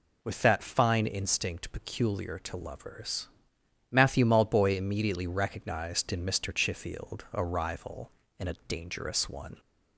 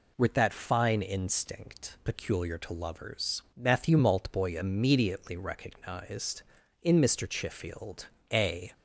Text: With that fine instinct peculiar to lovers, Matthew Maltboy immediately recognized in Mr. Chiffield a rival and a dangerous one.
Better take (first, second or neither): first